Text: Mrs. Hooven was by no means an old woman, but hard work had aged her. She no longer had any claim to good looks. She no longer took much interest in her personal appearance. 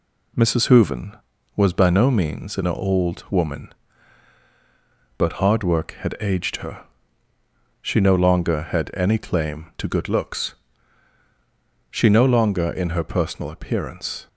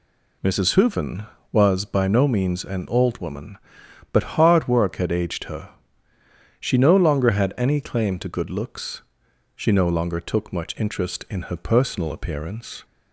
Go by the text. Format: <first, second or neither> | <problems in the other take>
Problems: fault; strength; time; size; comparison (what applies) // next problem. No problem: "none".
second | skips "took much interest"; at 12.6 s